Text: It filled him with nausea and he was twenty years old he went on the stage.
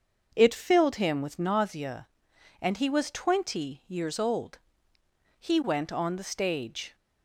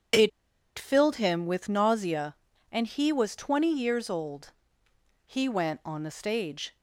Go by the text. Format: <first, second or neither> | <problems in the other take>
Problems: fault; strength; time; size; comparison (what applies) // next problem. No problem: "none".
first | starts louder than the rest; strong; until 1.6 s; 8 dB; also in the first // pauses between "It" and "filled"; noticeable; at 0.3 s; 0.48 s long // pauses between "old" and "he"; noticeable; at 4.5 s; 0.72 s long; noticeable in the first